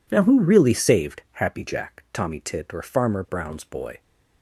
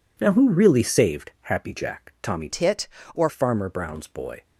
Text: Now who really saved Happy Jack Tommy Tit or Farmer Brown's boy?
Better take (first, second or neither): first